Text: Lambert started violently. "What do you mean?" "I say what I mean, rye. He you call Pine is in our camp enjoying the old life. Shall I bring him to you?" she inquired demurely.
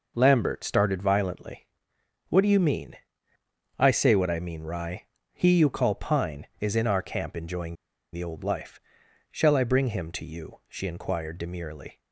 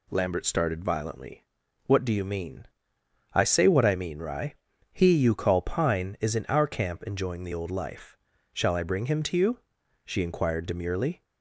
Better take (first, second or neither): second